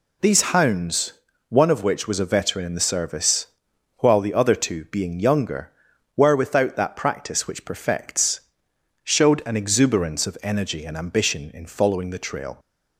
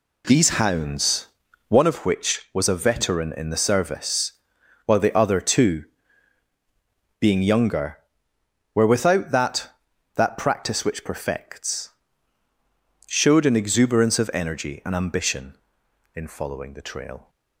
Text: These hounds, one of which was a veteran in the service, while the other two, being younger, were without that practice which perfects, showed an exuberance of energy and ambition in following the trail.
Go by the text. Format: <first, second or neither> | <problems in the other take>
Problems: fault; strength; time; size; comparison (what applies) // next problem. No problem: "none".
first | says "that" twice; at 10.1 s